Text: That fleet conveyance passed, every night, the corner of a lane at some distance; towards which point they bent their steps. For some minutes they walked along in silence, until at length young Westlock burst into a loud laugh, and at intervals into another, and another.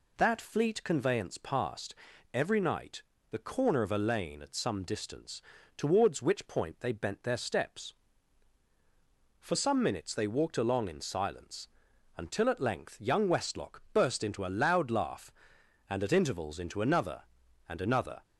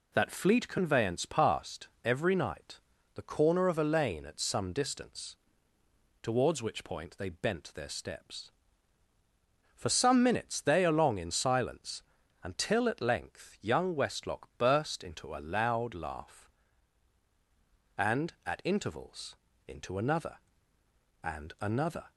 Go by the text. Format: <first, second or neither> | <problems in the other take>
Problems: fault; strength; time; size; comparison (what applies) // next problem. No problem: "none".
first | skips "walked"; at 10.8 s // pauses between "intervals" and "into"; slight; at 19.3 s; 0.30 s long